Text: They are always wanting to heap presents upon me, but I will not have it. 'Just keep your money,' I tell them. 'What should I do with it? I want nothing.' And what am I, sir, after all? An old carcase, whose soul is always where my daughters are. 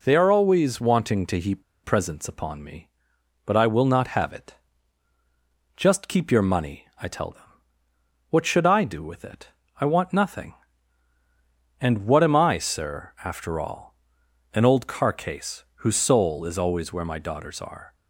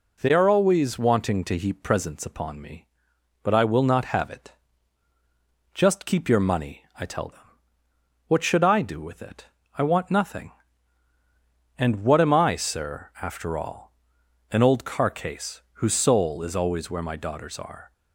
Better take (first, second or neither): second